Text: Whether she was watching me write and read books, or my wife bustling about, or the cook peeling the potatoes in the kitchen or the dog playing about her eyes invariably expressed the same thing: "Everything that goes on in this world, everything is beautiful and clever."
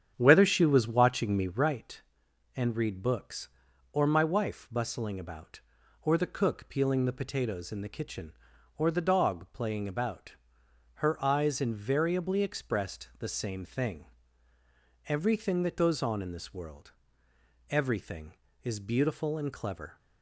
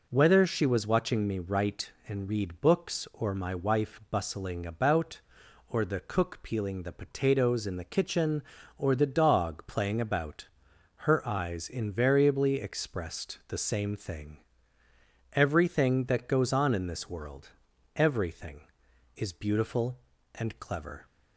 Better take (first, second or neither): second